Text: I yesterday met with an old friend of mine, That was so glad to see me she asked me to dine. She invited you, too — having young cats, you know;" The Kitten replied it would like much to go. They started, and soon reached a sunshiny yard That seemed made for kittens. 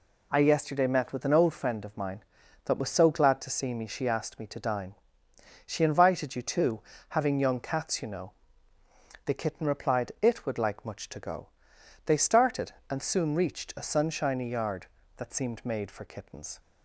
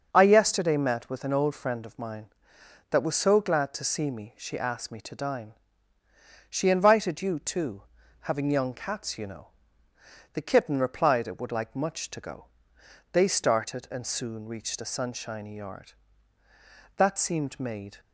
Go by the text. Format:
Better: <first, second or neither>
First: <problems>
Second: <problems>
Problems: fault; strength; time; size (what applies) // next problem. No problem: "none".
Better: first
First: none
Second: starts louder than the rest; until 1.1 s; 6.5 dB // stops before "for kittens"; at 17.9 s